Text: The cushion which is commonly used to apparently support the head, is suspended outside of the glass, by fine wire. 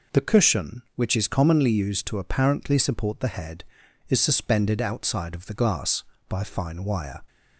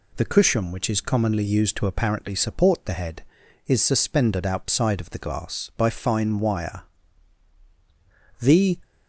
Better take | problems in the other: first | goes on to say "The"; slight; from 8.3 s on; 0.38 s long

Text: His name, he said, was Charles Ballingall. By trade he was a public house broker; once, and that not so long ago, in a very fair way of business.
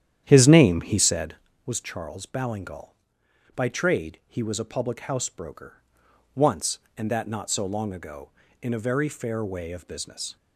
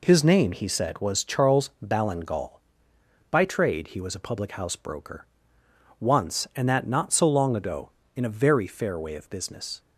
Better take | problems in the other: second | starts louder than the rest; strong; until 1.5 s; 10.5 dB

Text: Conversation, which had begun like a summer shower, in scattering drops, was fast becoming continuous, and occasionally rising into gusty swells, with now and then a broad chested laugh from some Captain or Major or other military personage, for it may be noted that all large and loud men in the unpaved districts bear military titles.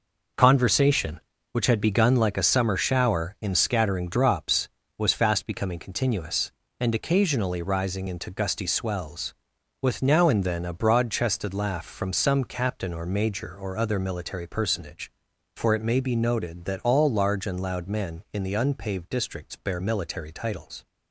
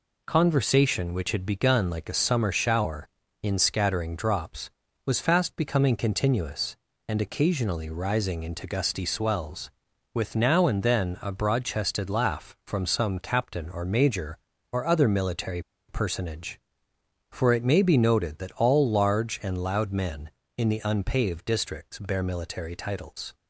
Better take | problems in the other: first | pauses between "military" and "personage"; slight; at 15.6 s; 0.27 s long

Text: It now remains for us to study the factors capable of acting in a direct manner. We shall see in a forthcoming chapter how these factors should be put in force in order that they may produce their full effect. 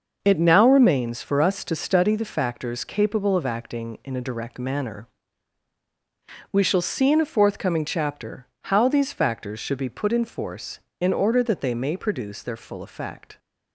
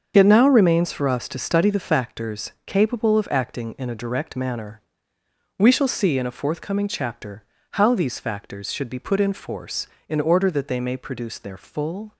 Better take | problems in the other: first | starts louder than the rest; until 1.1 s; 6.5 dB; noticeable in the first // pauses between "chapter" and "how"; slight; at 7.4 s; 0.28 s long; slight in the first // stops before "effect"; at 12.1 s

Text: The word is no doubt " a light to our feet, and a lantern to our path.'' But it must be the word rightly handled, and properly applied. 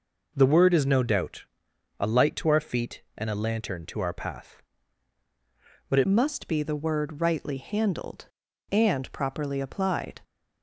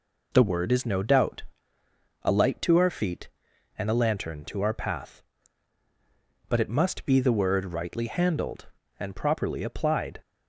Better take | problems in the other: second | changes voice at "must"; from 6.0 s on; 4.2 s long

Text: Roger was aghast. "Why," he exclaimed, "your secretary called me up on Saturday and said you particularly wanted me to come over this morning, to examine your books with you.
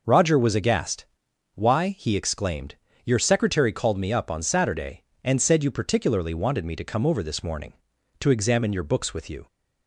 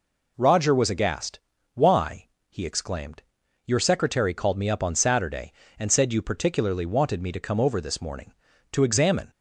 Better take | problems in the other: first | stops before "your books with you"; at 9.3 s

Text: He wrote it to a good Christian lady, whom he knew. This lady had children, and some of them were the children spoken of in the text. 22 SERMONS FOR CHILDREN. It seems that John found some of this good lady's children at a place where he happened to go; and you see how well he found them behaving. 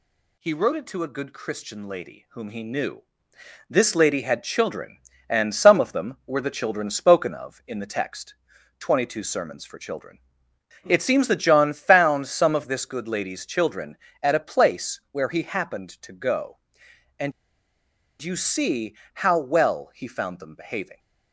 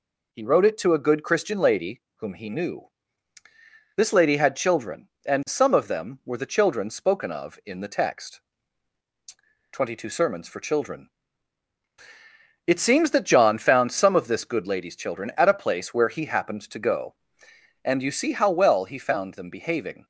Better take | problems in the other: second | pauses between "and" and "you"; noticeable; at 17.3 s; 0.90 s long // pauses between "see" and "how"; slight; at 18.9 s; 0.20 s long

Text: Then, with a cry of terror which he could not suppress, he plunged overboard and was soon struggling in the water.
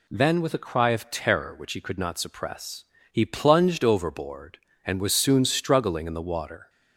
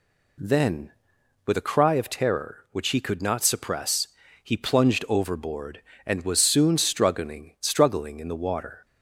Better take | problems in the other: first | says "struggling" twice; at 7.5 s

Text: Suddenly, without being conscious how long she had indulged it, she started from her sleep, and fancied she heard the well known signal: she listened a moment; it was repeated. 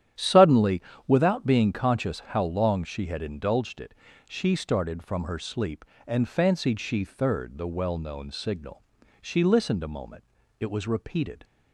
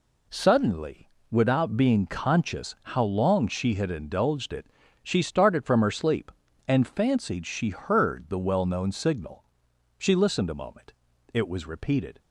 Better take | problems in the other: second | starts louder than the rest; strong; until 1.4 s; 10.5 dB // says "third" for "heard"; at 7.0 s

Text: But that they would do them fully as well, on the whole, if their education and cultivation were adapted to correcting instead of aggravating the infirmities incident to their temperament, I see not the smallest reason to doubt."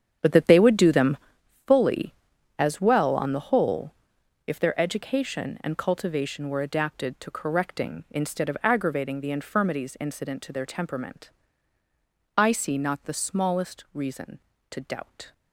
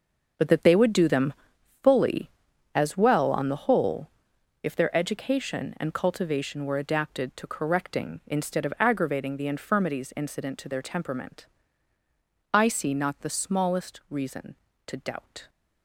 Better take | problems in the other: second | starts louder than the rest; strong; until 1.4 s; 8.5 dB // pauses between "them" and "fully"; noticeable; at 1.1 s; 0.50 s long; noticeable in the second

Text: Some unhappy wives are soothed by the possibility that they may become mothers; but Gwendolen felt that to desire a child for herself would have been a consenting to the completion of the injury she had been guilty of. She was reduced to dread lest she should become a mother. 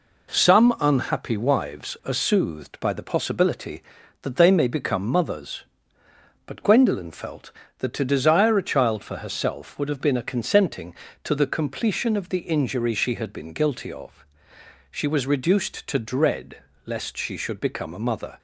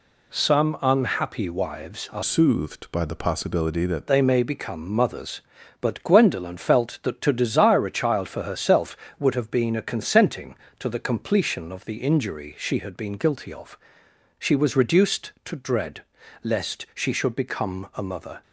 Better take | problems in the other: first | changes voice from "soothed" to "that"; from 2.2 to 4.0 s; 1.8 s long // pauses between "dread" and "lest"; at 16.0 s; 0.40 s long; slight in the first

